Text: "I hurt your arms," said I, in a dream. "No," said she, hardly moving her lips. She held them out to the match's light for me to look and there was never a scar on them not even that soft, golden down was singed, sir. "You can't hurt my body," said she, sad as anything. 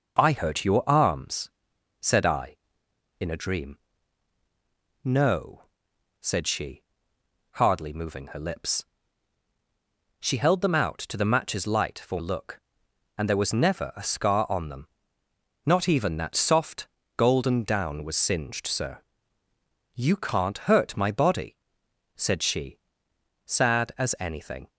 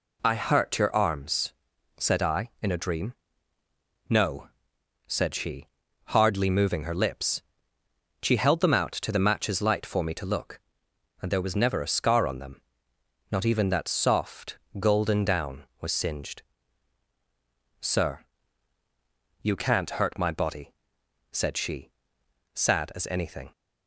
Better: second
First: skips "me to"; at 12.1 s // pauses between "them" and "not"; noticeable; at 14.8 s; 0.76 s long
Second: pauses between "them" and "not"; noticeable; at 12.6 s; 0.70 s long

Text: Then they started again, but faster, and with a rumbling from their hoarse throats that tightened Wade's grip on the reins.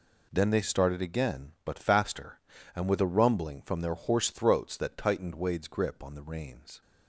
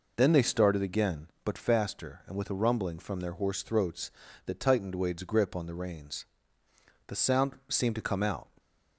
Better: first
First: none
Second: goes on to say "The sound seemed to come out"; from 7.0 s on; 1.4 s long

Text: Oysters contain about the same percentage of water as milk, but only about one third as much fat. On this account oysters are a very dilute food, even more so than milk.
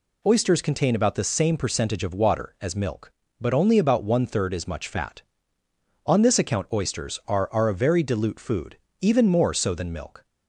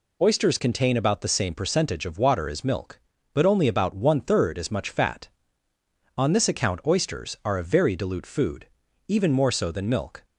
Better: second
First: says "are" twice; at 7.5 s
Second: none

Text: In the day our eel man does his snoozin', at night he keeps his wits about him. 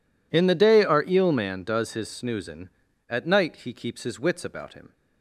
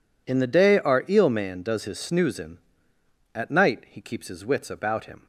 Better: neither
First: none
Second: none

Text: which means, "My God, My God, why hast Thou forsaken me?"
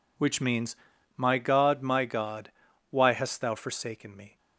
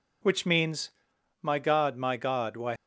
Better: first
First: none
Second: stops before "hast Thou forsaken me"; at 2.7 s

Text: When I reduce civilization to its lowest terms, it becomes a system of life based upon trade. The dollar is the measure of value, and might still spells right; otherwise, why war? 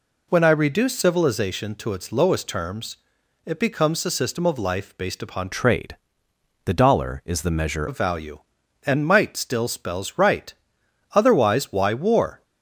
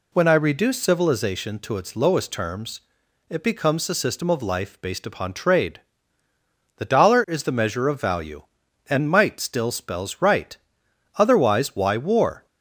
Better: second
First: changes voice from "trade" to "measure"; from 5.5 to 7.8 s; 2.3 s long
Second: none

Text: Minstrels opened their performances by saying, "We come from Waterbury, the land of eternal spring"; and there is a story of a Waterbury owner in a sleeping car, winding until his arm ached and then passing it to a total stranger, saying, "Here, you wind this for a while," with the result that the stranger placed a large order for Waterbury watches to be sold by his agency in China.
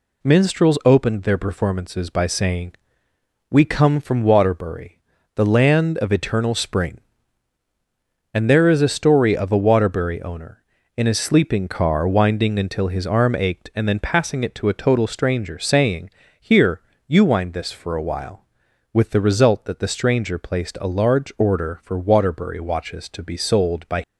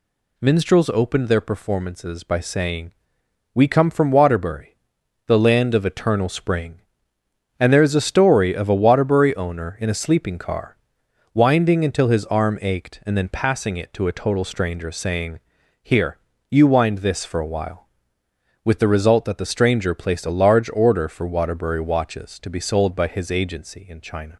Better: second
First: stops before "his agency in China"; at 24.0 s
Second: none

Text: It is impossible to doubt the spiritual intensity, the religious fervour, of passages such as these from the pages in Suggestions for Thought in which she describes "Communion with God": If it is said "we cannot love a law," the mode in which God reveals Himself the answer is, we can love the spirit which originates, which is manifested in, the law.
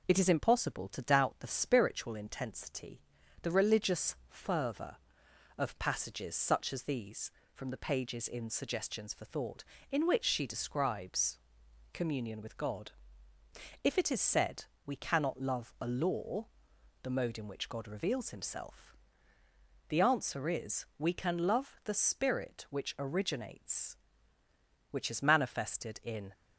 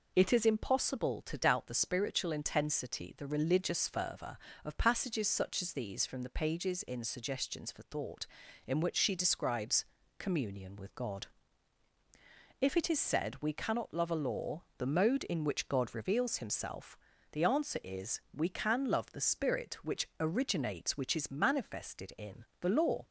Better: second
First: pauses between "describes" and "Communion"; noticeable; at 11.3 s; 0.56 s long // pauses between "said" and "we"; slight; at 14.6 s; 0.20 s long // pauses between "Himself" and "the"; noticeable; at 18.9 s; 0.96 s long // stops before "the law"; at 26.3 s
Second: pauses between "describes" and "Communion"; slight; at 9.8 s; 0.34 s long // pauses between "Himself" and "the"; slight; at 16.9 s; 0.32 s long

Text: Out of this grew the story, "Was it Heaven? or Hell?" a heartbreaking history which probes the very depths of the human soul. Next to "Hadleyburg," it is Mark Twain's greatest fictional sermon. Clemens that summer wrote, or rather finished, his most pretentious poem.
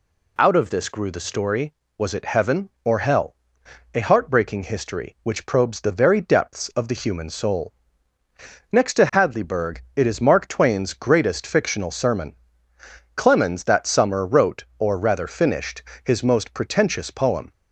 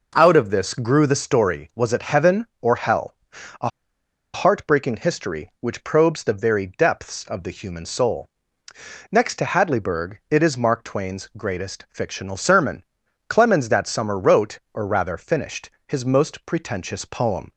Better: first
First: none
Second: pauses between "a" and "heartbreaking"; noticeable; at 3.6 s; 0.66 s long

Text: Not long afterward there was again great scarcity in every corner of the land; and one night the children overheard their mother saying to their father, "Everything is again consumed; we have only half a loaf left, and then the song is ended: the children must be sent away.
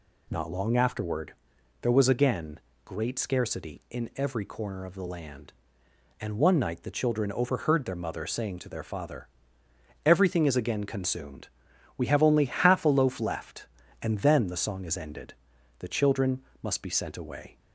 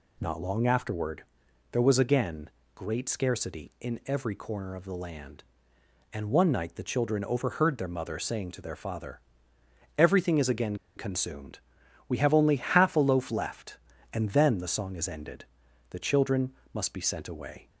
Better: first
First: pauses between "afterward" and "there"; noticeable; at 1.3 s; 0.48 s long // pauses between "again" and "great"; slight; at 2.5 s; 0.26 s long // pauses between "children" and "must"; slight; at 16.4 s; 0.18 s long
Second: pauses between "afterward" and "there"; noticeable; at 1.2 s; 0.48 s long // pauses between "again" and "great"; slight; at 2.4 s; 0.26 s long // pauses between "again" and "consumed"; slight; at 10.7 s; 0.21 s long // pauses between "children" and "must"; slight; at 16.5 s; 0.18 s long

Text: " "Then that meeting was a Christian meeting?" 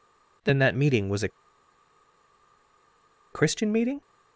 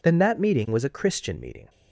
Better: second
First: pauses between "a" and "Christian"; strong; at 1.2 s; 2.0 s long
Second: none

